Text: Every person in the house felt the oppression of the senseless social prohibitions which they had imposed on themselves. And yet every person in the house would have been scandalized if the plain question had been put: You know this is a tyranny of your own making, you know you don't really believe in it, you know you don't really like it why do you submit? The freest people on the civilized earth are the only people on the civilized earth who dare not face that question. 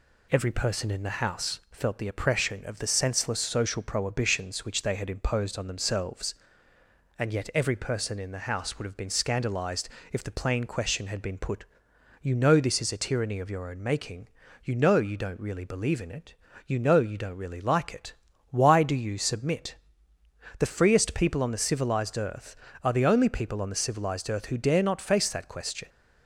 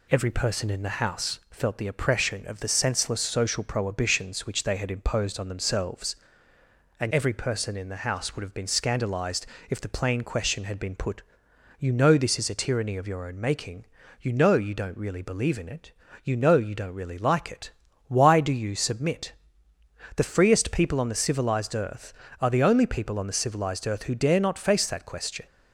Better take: first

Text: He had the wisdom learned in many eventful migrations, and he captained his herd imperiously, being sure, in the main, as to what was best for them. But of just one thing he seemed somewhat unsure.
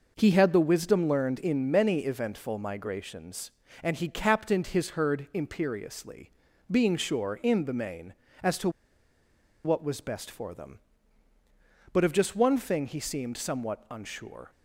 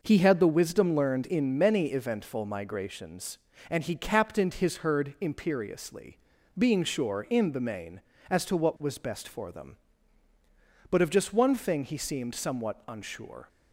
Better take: second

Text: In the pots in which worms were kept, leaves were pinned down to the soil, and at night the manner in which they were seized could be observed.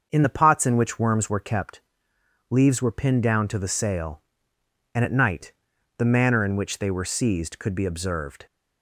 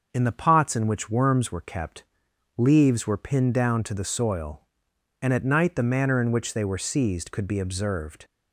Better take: second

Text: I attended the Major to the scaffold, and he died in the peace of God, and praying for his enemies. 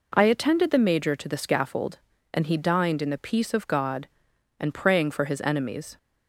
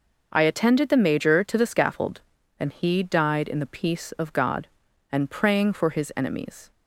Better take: second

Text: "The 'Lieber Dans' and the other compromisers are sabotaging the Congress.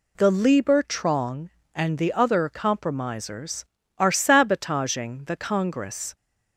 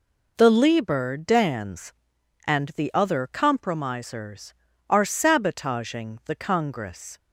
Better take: second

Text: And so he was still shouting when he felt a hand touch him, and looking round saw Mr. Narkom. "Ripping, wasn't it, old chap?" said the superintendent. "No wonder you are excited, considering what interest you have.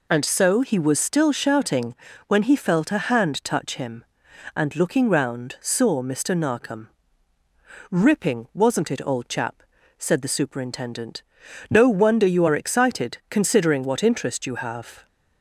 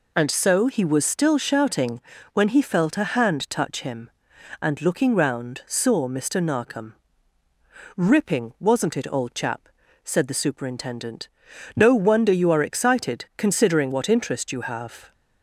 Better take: neither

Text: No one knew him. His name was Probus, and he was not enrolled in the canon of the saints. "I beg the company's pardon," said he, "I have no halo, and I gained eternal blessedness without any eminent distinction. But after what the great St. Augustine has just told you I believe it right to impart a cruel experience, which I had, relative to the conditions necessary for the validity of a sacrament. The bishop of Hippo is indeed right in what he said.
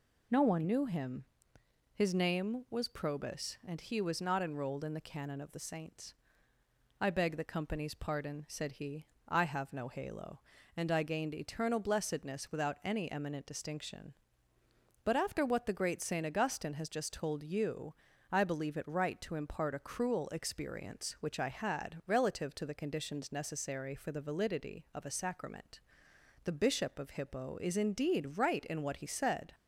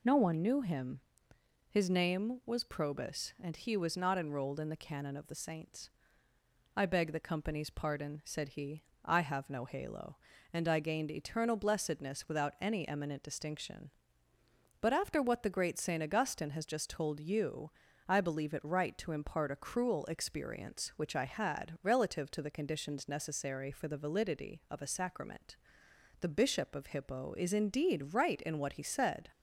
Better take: neither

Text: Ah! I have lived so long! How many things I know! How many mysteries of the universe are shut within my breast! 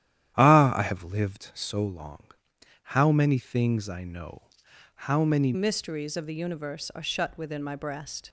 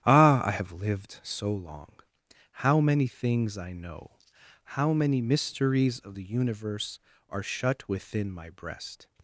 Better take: second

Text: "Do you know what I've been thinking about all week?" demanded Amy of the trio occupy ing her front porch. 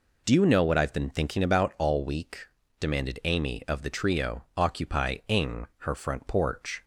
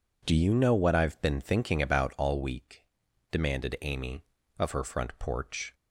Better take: first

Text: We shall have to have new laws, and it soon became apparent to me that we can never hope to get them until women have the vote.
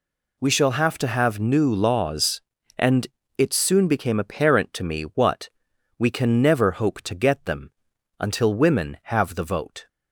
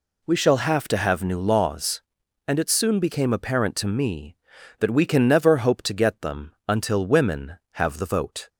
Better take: second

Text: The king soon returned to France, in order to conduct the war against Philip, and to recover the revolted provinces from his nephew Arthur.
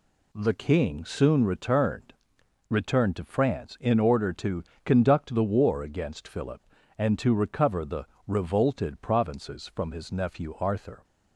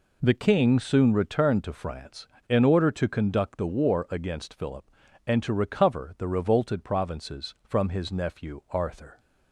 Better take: second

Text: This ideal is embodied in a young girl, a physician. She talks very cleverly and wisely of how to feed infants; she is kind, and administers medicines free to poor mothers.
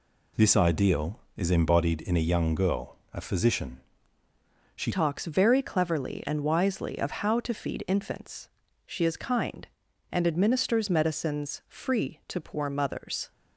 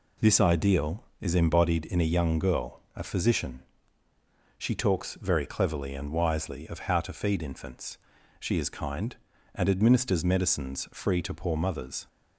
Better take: second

